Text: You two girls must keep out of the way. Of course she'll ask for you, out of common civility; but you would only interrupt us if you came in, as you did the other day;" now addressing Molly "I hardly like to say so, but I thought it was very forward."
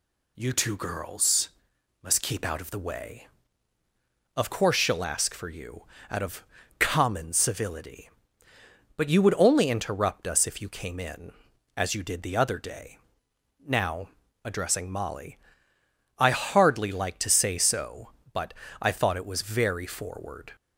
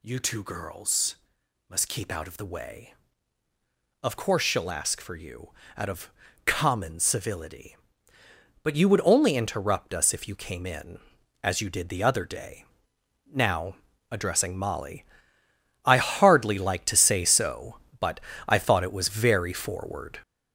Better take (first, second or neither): first